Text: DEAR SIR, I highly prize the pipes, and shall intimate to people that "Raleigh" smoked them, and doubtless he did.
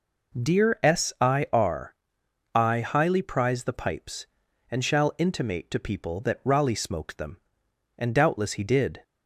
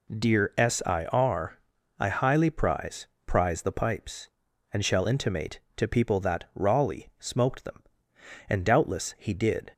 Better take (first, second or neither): first